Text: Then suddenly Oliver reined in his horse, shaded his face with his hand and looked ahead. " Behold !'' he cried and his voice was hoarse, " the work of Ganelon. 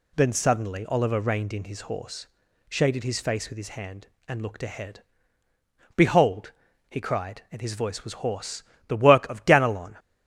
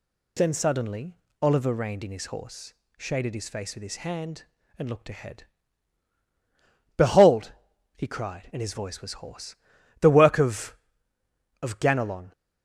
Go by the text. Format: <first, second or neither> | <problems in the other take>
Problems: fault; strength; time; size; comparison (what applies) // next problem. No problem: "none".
first | pauses between "suddenly" and "Oliver"; slight; at 1.1 s; 0.24 s long // says "of" twice; at 11.6 s